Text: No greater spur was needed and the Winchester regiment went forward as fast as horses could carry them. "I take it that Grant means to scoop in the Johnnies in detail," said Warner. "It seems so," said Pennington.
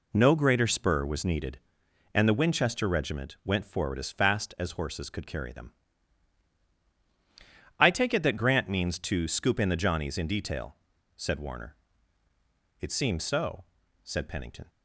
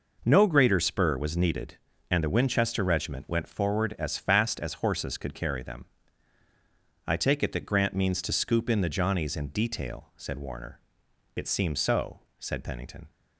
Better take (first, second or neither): neither